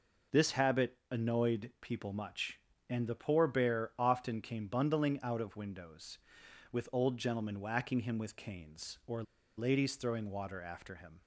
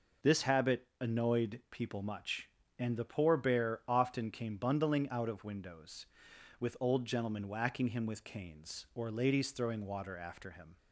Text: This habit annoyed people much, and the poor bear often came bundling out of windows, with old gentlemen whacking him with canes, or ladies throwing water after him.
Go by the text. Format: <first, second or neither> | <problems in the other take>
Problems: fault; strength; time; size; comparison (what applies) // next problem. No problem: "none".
second | pauses between "or" and "ladies"; slight; at 9.2 s; 0.34 s long